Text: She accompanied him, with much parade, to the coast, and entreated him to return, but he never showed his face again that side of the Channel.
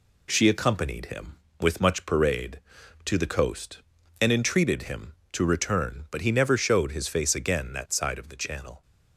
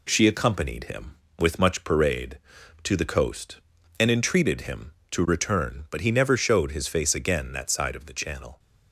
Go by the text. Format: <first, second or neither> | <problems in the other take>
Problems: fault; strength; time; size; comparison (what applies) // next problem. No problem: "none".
neither | none